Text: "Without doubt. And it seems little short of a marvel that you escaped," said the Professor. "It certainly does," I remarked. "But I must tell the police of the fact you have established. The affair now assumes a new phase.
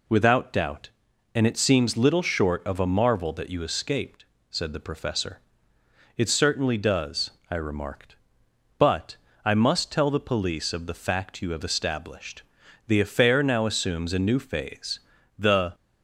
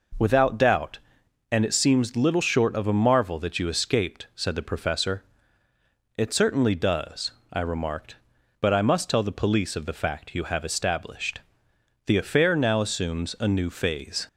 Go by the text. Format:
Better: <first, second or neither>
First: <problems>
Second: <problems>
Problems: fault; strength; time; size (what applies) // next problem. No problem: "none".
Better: second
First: pauses between "But" and "I"; slight; at 9.1 s; 0.28 s long // goes on to say "The"; slight; from 15.3 s on; 0.38 s long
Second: none